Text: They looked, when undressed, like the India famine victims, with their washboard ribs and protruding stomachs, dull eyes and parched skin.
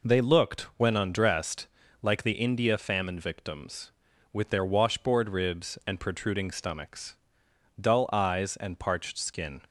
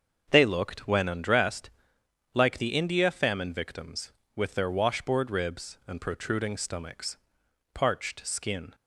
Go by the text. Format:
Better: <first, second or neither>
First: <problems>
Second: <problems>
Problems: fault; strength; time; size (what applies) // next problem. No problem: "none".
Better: first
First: none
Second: starts louder than the rest; until 1.3 s; 6.5 dB // skips "dull eyes and"; at 7.4 s